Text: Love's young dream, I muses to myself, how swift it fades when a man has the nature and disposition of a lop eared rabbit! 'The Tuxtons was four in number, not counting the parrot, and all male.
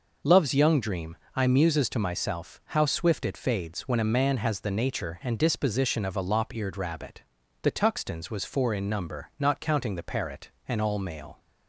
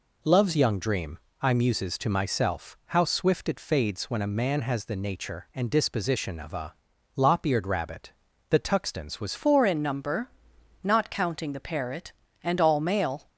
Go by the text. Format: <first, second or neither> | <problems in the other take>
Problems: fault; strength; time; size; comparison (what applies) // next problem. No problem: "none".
first | pauses between "a" and "lop"; at 6.7 s; 0.42 s long // changes voice at "four"; from 9.3 s on; 3.9 s long